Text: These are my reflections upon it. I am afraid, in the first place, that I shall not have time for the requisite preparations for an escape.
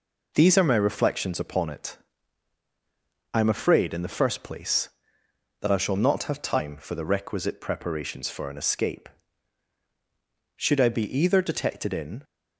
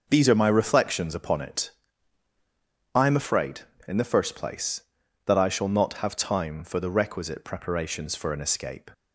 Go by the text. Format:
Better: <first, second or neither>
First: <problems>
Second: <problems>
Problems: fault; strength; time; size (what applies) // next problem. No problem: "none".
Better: second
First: goes on to say "Should I be either detected in"; strong; from 10.5 s on; 1.6 s long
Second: none